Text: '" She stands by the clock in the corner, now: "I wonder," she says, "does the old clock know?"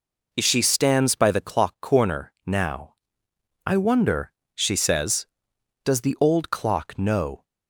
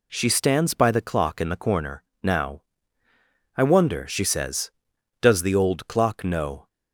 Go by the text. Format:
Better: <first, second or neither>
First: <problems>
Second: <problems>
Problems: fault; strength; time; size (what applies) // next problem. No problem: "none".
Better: second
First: skips "in the"; at 1.7 s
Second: none